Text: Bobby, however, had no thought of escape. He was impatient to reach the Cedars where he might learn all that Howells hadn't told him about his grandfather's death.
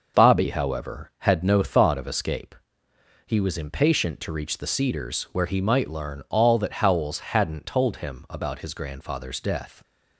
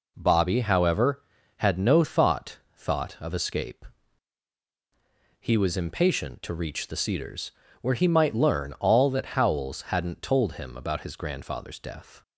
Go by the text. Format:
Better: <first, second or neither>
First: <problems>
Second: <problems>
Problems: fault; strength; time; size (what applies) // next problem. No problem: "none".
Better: first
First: none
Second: says "thought" twice; at 2.7 s // pauses between "Cedars" and "where"; slight; at 7.5 s; 0.30 s long